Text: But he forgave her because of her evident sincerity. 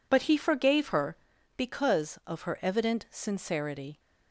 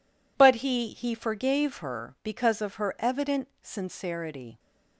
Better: first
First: none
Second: says "he" twice; at 0.8 s // pauses between "evident" and "sincerity"; slight; at 3.4 s; 0.16 s long

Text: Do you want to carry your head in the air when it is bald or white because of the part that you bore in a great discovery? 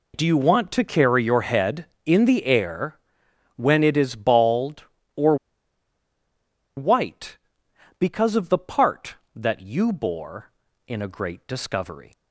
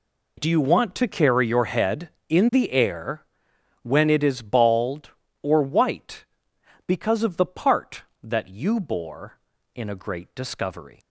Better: second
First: pauses between "air" and "when"; noticeable; at 2.9 s; 0.58 s long // pauses between "or" and "white"; strong; at 5.3 s; 1.4 s long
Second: pauses between "air" and "when"; noticeable; at 3.2 s; 0.58 s long

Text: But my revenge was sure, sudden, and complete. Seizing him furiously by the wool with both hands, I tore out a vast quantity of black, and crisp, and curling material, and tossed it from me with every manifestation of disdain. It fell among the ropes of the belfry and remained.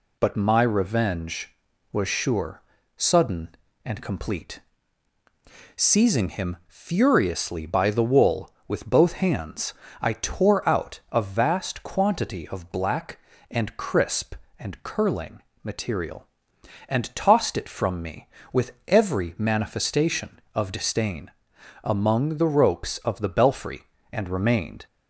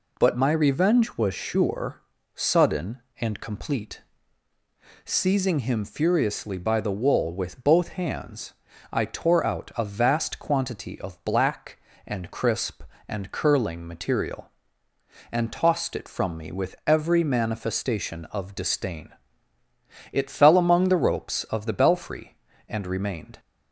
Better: second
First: pauses between "curling" and "material"; slight; at 15.3 s; 0.22 s long // pauses between "with" and "every"; slight; at 18.7 s; 0.16 s long // skips "It fell"; at 21.5 s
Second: none

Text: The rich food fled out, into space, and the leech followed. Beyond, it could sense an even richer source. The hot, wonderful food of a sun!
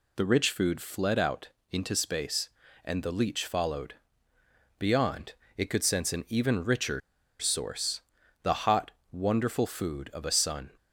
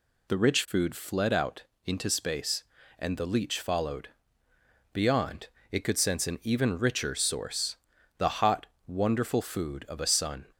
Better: second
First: pauses between "richer" and "source"; at 6.9 s; 0.40 s long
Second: none

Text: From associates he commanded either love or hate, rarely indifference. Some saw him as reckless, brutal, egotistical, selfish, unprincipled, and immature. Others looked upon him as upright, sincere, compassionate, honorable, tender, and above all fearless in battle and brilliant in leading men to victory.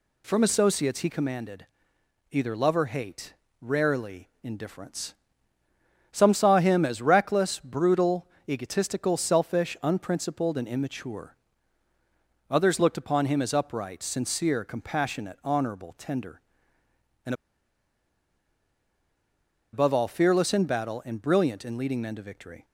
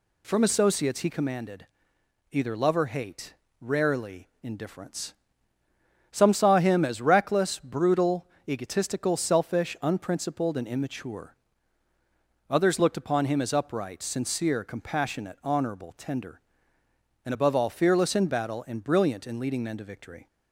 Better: second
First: pauses between "commanded" and "either"; noticeable; at 1.6 s; 0.64 s long // pauses between "and" and "above"; strong; at 17.3 s; 2.3 s long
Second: pauses between "commanded" and "either"; noticeable; at 1.6 s; 0.64 s long

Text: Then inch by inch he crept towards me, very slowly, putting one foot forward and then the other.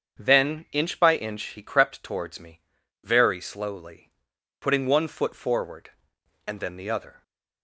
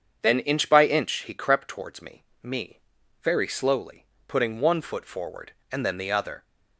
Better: first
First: starts louder than the rest; strong; until 1.2 s; 7.5 dB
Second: starts louder than the rest; strong; until 1.2 s; 7 dB // says "me" twice; at 2.4 s

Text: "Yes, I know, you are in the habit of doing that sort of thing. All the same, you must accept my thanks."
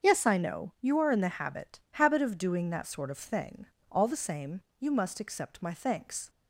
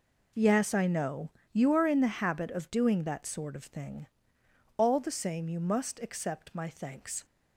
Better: second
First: starts louder than the rest; until 1.1 s; 7 dB // says "habit" twice; at 1.9 s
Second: none

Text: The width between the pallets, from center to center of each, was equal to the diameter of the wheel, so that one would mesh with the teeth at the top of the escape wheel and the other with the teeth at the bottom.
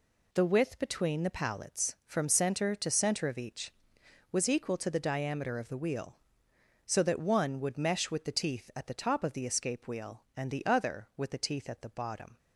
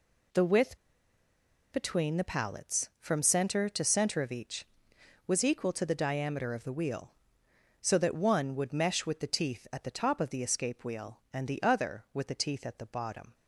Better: first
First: none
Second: pauses between "width" and "between"; noticeable; at 0.7 s; 0.95 s long

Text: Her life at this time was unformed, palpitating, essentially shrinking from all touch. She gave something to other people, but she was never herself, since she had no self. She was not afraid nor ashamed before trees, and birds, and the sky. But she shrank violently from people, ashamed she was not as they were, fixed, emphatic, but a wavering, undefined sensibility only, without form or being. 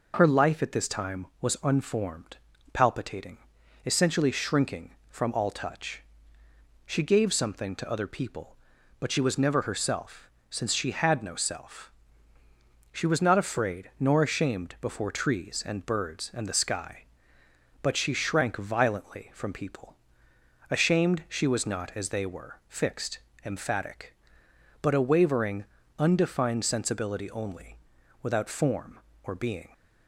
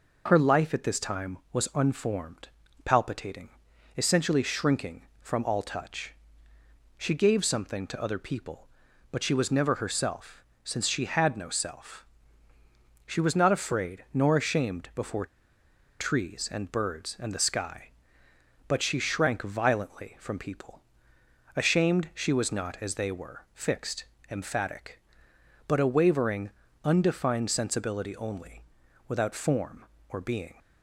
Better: first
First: none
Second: pauses between "before" and "trees"; noticeable; at 15.2 s; 0.74 s long

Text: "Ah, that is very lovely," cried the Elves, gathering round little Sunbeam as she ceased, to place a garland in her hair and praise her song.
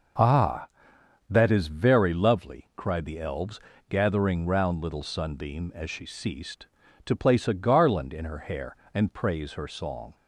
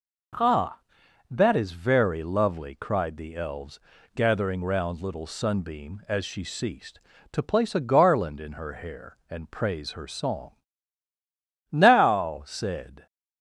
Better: first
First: none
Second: goes on to say "Now said"; from 11.7 s on; 1.3 s long

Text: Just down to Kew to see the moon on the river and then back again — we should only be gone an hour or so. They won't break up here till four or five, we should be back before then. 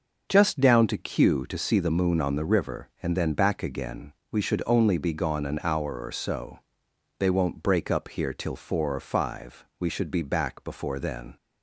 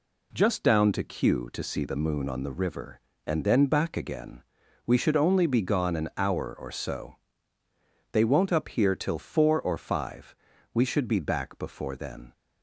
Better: first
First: none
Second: skips "break"; at 8.5 s

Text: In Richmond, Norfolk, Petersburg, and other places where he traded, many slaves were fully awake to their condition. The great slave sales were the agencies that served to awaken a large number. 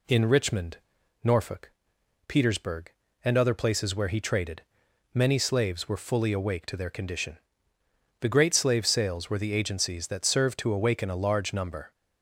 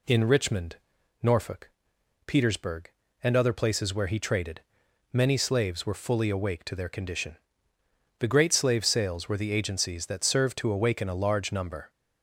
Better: neither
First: none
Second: none

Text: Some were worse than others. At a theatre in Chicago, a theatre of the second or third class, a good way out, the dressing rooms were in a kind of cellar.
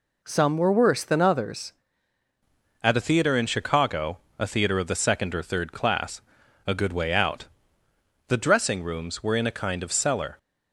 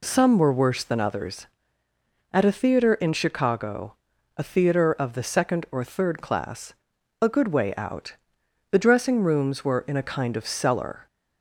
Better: second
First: changes voice at "At"; from 2.8 s on; 7.5 s long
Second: none

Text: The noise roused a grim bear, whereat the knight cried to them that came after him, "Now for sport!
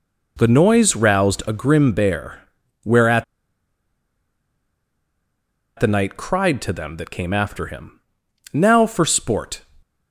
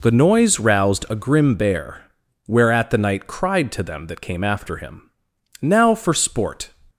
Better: second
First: pauses between "whereat" and "the"; strong; at 3.2 s; 2.5 s long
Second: none

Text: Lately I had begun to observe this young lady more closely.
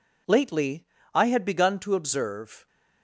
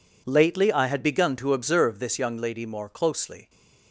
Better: second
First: pauses between "Lately" and "I"; slight; at 0.8 s; 0.30 s long // stops before "this young lady more closely"; at 2.6 s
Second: none

